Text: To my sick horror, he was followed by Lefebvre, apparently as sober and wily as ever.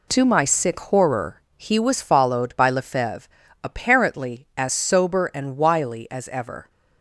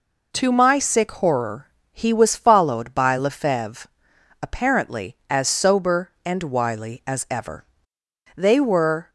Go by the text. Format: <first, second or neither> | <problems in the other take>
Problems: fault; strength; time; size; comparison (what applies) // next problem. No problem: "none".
first | goes on to say "They were"; noticeable; from 8.3 s on; 0.74 s long